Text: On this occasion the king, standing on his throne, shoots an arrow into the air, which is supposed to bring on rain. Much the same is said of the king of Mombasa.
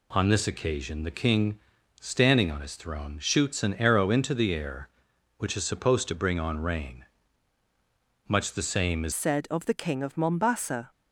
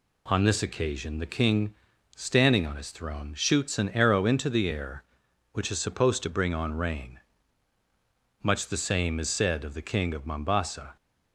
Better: second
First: changes voice at "said"; from 9.1 s on; 1.8 s long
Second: none

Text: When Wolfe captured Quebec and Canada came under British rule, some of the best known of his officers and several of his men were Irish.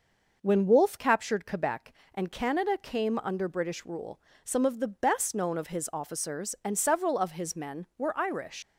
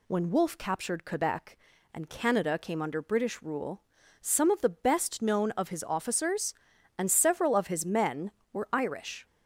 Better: second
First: leaves "Irish" unfinished; at 8.6 s; 90 ms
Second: none

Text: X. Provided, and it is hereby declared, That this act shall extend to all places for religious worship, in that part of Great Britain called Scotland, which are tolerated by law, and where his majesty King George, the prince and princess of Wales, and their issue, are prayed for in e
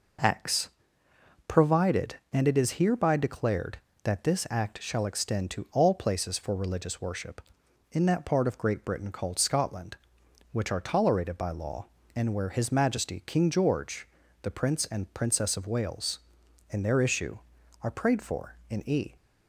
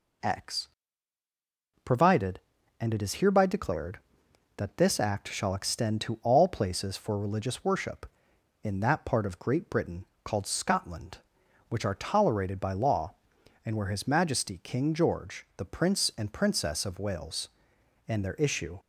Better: first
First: none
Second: pauses between "Britain" and "called"; slight; at 10.0 s; 0.20 s long // stops before "are prayed for in e"; at 18.7 s

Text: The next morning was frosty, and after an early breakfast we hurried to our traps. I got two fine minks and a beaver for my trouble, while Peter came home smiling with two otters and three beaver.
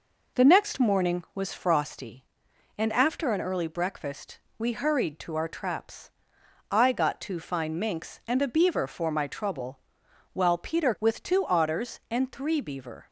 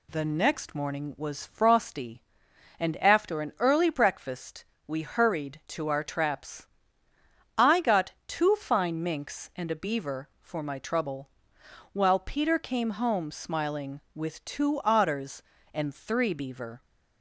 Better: second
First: pauses between "breakfast" and "we"; slight; at 4.3 s; 0.18 s long // skips "came home smiling"; at 10.9 s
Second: pauses between "breakfast" and "we"; slight; at 4.6 s; 0.24 s long

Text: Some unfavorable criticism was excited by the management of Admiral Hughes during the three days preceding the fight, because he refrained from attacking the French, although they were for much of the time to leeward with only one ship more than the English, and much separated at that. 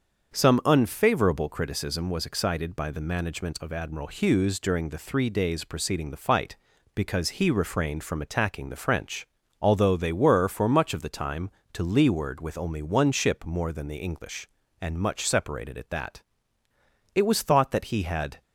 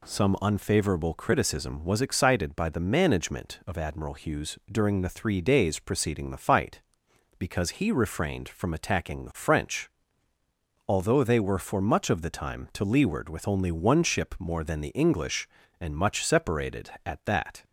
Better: second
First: starts louder than the rest; until 1.3 s; 7 dB // goes on to say "It was thought that he had"; noticeable; from 17.1 s on; 1.2 s long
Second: none

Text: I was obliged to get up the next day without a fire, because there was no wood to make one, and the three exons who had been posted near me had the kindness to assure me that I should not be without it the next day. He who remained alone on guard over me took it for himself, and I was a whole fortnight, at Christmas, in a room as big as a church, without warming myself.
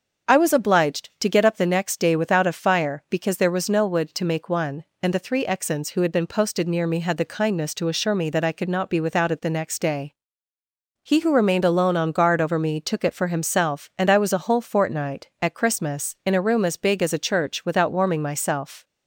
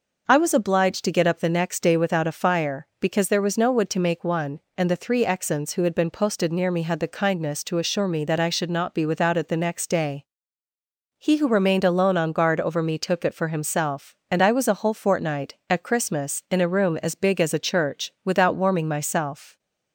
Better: second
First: starts louder than the rest; until 1.3 s; 6.5 dB // says "could" for "should"; at 8.5 s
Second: none

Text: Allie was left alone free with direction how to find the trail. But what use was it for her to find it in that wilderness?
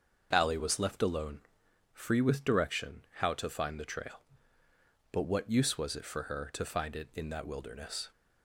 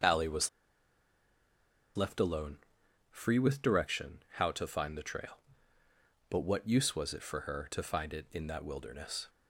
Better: first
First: starts louder than the rest; noticeable; until 1.3 s; 6 dB // pauses between "alone" and "free"; noticeable; at 1.4 s; 0.52 s long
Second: starts louder than the rest; until 2.5 s; 6.5 dB // pauses between "was" and "left"; strong; at 0.4 s; 1.4 s long // pauses between "alone" and "free"; noticeable; at 2.5 s; 0.52 s long

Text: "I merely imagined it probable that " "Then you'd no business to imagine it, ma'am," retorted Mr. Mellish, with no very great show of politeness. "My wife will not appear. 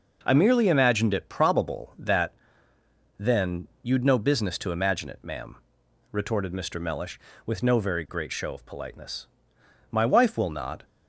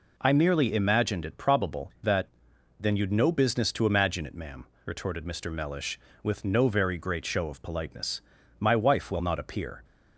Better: second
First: pauses between "Then" and "you'd"; slight; at 3.6 s; 0.16 s long // stops before "appear"; at 10.8 s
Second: none

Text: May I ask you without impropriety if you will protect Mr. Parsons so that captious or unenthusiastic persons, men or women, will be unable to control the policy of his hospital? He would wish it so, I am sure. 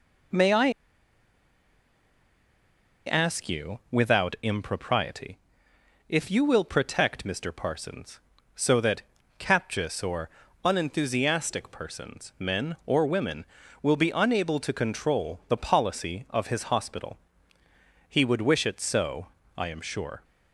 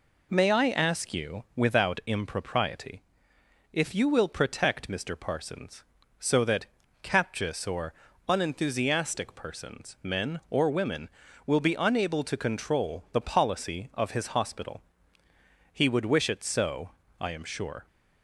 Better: second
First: pauses between "I" and "ask"; strong; at 0.6 s; 2.3 s long // pauses between "impropriety" and "if"; noticeable; at 5.3 s; 0.72 s long // pauses between "that" and "captious"; slight; at 9.0 s; 0.34 s long // pauses between "or" and "unenthusiastic"; slight; at 10.2 s; 0.34 s long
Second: pauses between "impropriety" and "if"; noticeable; at 3.0 s; 0.72 s long // pauses between "that" and "captious"; slight; at 6.6 s; 0.34 s long // pauses between "or" and "unenthusiastic"; slight; at 7.9 s; 0.34 s long

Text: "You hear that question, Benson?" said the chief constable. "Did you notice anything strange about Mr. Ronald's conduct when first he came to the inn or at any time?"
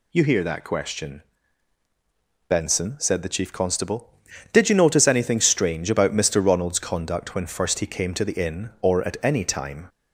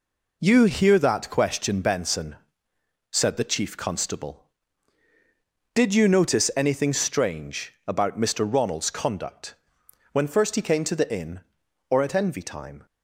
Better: first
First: none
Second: pauses between "conduct" and "when"; noticeable; at 9.5 s; 0.58 s long // says "envy" for "any"; at 12.1 s

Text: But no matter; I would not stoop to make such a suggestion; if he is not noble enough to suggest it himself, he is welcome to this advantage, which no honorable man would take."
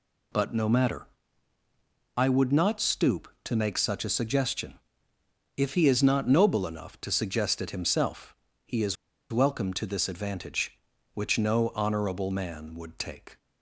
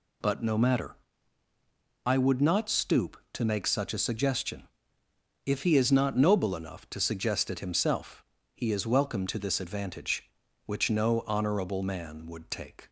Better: second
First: pauses between "is" and "welcome"; slight; at 8.9 s; 0.35 s long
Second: none

